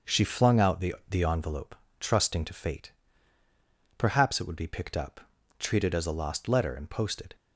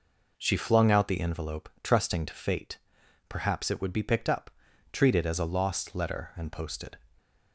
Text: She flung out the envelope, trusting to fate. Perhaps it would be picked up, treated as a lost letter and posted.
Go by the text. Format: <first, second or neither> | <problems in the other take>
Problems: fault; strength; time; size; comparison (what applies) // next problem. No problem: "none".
second | starts louder than the rest; until 1.2 s; 6.5 dB // says "the" twice; at 1.0 s